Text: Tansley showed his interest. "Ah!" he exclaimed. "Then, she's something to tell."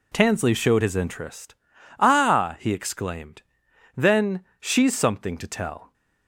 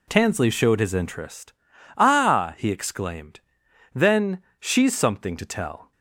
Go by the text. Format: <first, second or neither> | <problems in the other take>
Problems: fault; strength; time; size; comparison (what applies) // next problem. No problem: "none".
neither | none